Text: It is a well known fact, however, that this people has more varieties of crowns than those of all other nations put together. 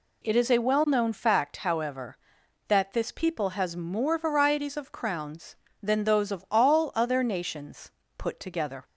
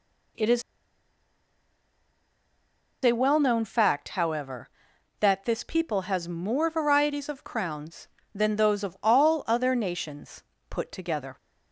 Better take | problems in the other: first | pauses between "is" and "a"; strong; at 0.6 s; 2.4 s long // pauses between "nations" and "put"; slight; at 10.4 s; 0.26 s long; slight in the first

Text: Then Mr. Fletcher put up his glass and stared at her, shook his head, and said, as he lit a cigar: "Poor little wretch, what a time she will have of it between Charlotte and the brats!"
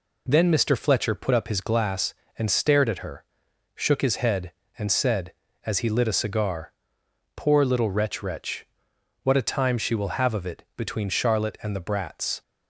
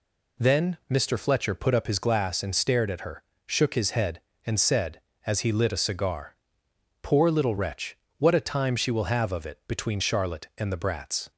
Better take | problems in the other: second | says "wretch" twice; at 8.2 s

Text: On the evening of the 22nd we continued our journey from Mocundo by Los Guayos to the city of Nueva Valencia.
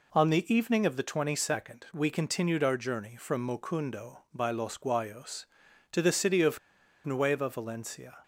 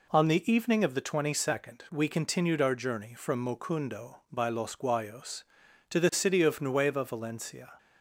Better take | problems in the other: second | pauses between "of" and "Nueva"; noticeable; at 6.5 s; 0.46 s long

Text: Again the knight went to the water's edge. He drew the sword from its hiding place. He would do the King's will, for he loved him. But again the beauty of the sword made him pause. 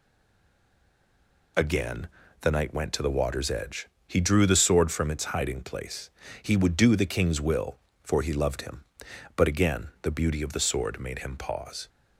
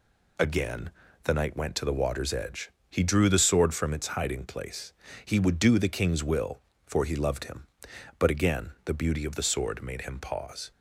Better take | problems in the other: second | stays silent before the first word; noticeable; until 1.5 s; 1.5 s long // pauses between "Again" and "the"; slight; at 2.0 s; 0.32 s long; slight in the second

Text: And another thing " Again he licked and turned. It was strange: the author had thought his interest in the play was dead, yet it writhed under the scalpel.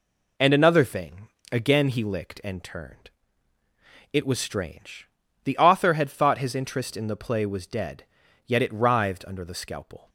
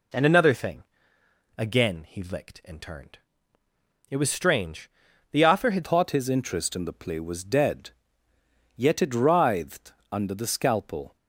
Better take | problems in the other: first | changes voice at "thought"; from 5.8 s on; 5.3 s long // pauses between "writhed" and "under"; slight; at 9.9 s; 0.18 s long

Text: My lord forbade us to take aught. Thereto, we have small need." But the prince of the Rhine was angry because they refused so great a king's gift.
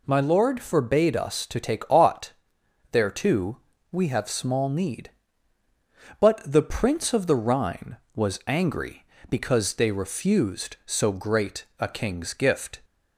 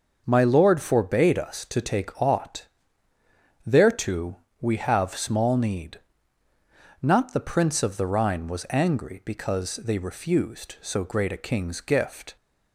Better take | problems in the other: first | starts louder than the rest; noticeable; until 1.2 s; 6 dB // says "Not" for "But"; at 7.0 s

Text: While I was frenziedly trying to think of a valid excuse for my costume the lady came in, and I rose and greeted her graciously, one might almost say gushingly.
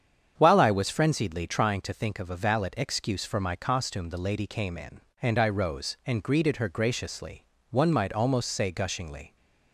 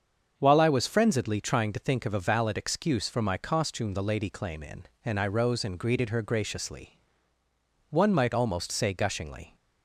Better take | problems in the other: first | starts louder than the rest; until 1.3 s; 7 dB; strong in the first // says "claim" for "came"; at 4.2 s

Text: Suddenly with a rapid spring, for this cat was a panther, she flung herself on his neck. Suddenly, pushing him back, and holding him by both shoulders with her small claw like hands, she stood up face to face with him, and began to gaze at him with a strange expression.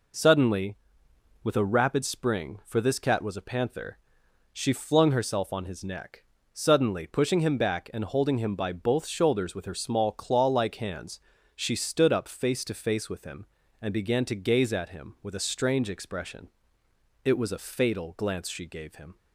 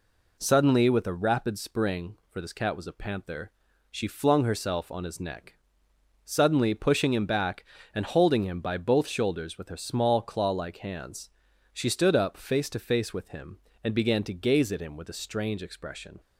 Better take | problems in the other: second | goes on to say "It was a fatal glance she gave him"; strong; from 17.2 s on; 1.9 s long

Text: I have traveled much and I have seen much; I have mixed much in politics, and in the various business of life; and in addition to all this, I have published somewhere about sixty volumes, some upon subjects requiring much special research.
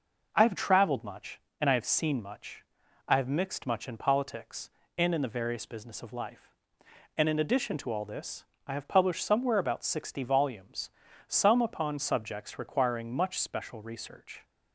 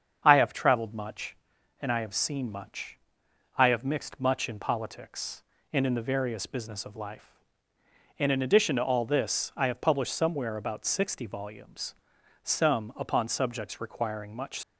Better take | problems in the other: first | starts louder than the rest; strong; until 1.2 s; 7 dB // stops before "special research"; at 14.6 s

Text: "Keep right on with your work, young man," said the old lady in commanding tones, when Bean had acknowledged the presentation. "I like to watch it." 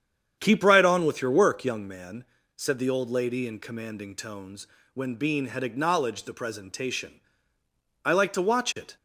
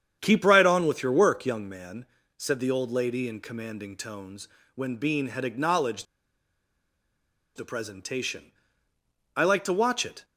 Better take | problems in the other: first | starts louder than the rest; strong; until 1.2 s; 8.5 dB; strong in the first // pauses between "acknowledged" and "the"; strong; at 6.0 s; 1.5 s long

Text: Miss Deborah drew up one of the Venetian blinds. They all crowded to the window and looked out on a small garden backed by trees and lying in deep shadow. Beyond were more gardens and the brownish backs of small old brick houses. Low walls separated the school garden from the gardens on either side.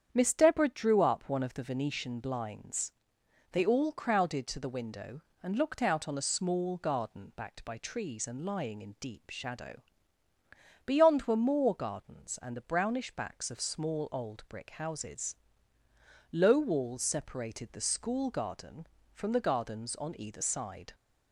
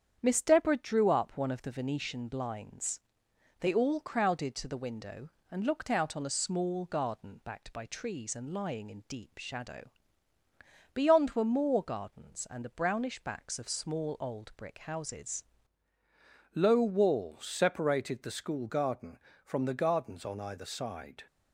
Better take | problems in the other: first | starts louder than the rest; strong; until 1.2 s; 8.5 dB; strong in the first // changes voice at "Low"; from 16.5 s on; 4.7 s long

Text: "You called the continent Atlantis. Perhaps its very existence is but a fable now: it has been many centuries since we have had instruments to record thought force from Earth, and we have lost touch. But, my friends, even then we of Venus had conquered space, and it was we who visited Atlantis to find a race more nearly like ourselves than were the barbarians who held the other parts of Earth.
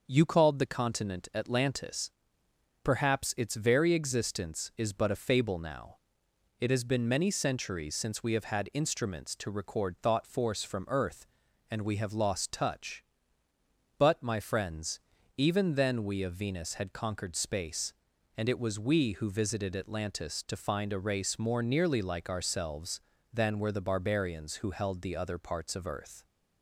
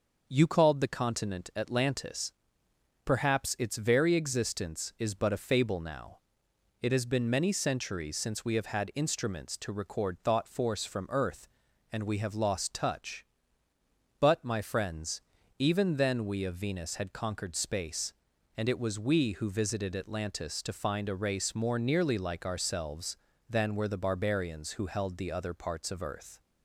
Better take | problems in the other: neither | starts louder than the rest; noticeable; the same in both

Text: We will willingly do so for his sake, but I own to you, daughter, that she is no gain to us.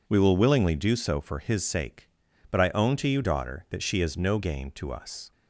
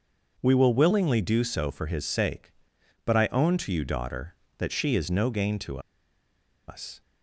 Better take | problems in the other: first | pauses between "to" and "us"; noticeable; at 5.7 s; 0.89 s long

